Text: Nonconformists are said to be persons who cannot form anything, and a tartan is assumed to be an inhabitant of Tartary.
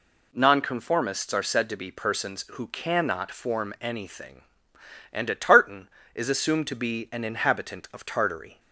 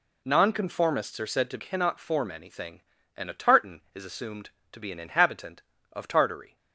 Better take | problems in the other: first | skips "be persons who"; at 1.5 s

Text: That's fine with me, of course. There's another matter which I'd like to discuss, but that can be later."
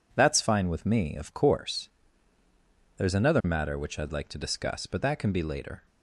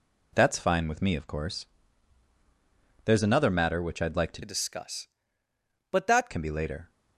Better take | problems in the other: first | changes voice from "discuss" to "that"; from 4.4 to 6.2 s; 1.8 s long

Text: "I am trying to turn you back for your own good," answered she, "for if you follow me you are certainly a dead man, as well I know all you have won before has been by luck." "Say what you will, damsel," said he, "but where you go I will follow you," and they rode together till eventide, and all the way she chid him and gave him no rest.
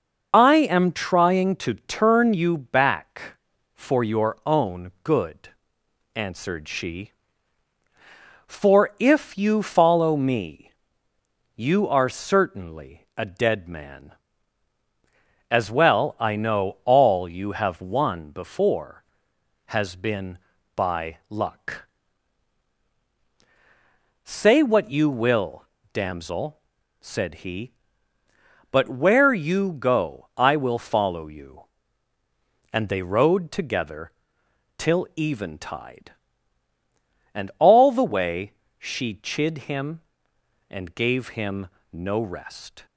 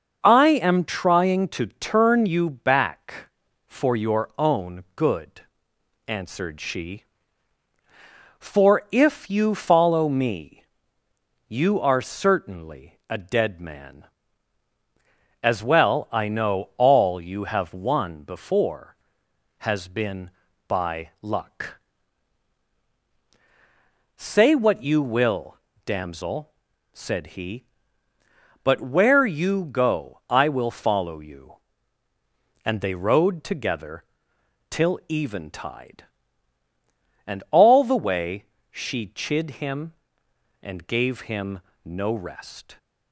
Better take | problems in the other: second | loses the start of "I"; at 0.3 s; 25 ms // starts louder than the rest; noticeable; until 1.3 s; 6 dB; also in the second // pauses between "me" and "you"; noticeable; at 10.7 s; 0.84 s long; noticeable in the second // pauses between "together" and "till"; noticeable; at 34.1 s; 0.66 s long; noticeable in the second // pauses between "way" and "she"; slight; at 38.5 s; 0.24 s long; slight in the second // pauses between "him" and "no"; slight; at 41.6 s; 0.24 s long; slight in the second

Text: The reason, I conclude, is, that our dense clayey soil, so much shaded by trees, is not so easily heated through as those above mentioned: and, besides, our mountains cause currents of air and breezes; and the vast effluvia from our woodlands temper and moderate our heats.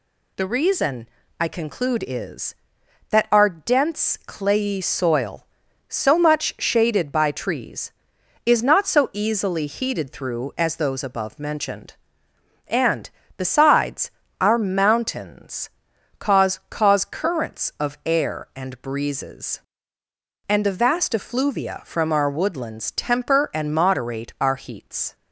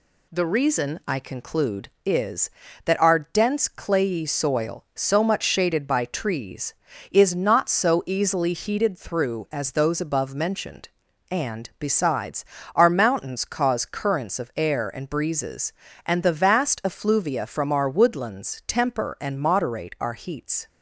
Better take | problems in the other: second | pauses between "mountains" and "cause"; noticeable; at 15.6 s; 0.50 s long // says "cause" twice; at 16.7 s

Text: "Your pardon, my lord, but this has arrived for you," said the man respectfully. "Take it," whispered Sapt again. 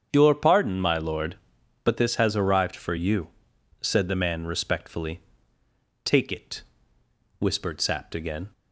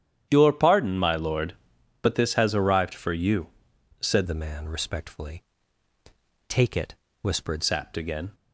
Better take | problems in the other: first | starts louder than the rest; strong; until 1.3 s; 10 dB; strong in the first // changes voice from "the" to "whispered"; from 4.2 to 7.6 s; 3.4 s long

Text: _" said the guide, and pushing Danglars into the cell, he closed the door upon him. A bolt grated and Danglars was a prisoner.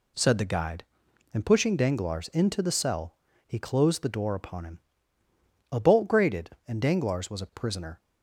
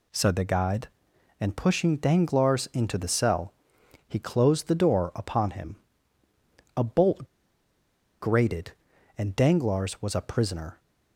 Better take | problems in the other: first | pauses between "bolt" and "grated"; noticeable; at 7.2 s; 0.93 s long

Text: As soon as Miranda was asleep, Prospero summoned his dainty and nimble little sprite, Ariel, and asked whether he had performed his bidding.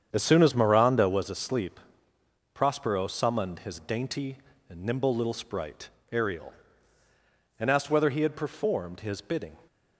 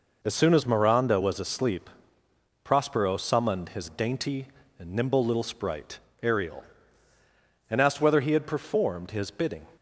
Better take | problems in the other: second | starts louder than the rest; strong; until 1.2 s; 8 dB

